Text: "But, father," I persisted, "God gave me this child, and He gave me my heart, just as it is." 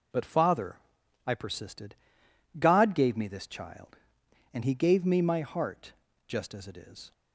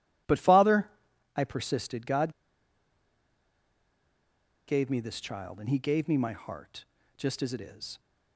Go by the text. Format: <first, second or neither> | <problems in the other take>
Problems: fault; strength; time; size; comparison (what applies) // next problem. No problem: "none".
first | pauses between "God" and "gave"; strong; at 2.3 s; 2.3 s long